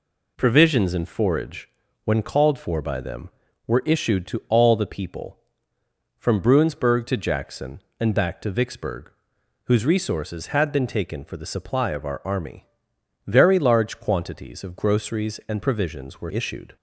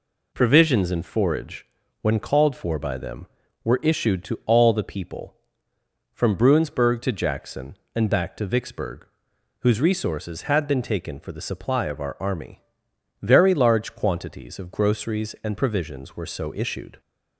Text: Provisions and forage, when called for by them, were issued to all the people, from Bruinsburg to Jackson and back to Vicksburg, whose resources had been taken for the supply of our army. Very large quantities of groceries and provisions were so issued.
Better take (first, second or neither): second